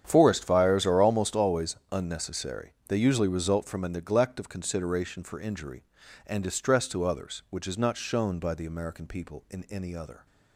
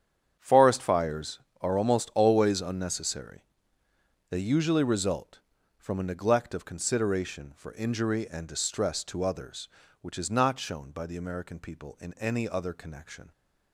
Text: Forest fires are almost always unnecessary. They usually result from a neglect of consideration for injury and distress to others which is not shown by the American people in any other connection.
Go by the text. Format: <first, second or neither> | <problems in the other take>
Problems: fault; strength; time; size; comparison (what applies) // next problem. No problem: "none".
second | starts louder than the rest; strong; until 1.0 s; 9 dB; strong in the second // pauses between "always" and "unnecessary"; slight; at 1.7 s; 0.16 s long // stops before "connection"; at 10.2 s